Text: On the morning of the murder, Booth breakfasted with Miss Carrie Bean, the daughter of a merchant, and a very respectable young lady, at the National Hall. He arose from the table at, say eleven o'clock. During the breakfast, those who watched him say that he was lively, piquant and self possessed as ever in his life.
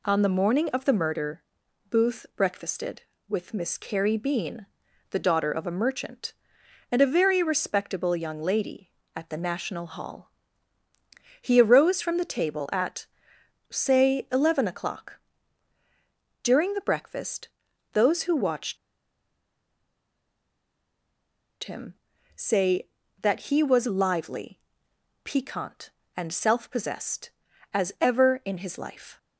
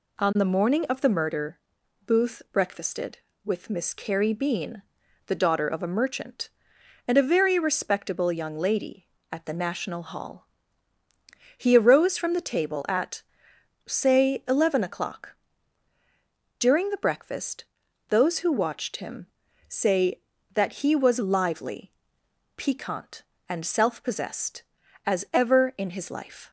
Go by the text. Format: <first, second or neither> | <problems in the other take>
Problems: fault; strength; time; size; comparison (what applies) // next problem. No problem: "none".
second | pauses between "watched" and "him"; strong; at 18.7 s; 2.8 s long // pauses between "him" and "say"; at 21.9 s; 0.40 s long; also in the second